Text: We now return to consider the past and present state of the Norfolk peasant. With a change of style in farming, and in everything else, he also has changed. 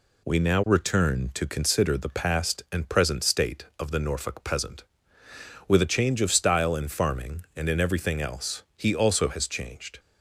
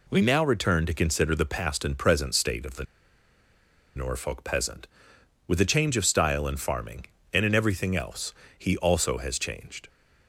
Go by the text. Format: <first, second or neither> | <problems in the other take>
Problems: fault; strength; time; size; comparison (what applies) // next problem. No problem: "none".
first | pauses between "the" and "Norfolk"; at 2.8 s; 1.1 s long